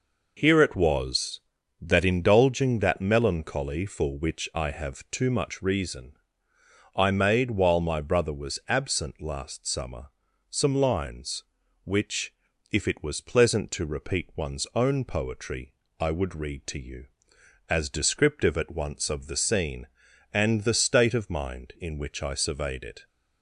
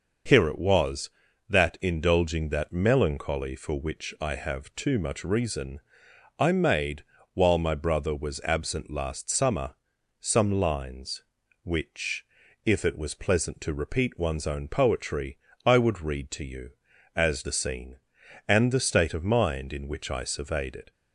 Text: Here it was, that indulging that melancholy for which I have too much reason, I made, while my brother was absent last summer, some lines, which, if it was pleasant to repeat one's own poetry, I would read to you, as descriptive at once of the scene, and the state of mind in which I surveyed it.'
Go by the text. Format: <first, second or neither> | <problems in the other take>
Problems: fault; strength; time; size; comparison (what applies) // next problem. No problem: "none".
first | starts louder than the rest; until 1.6 s; 6 dB // skips "descriptive at once of"; at 17.4 s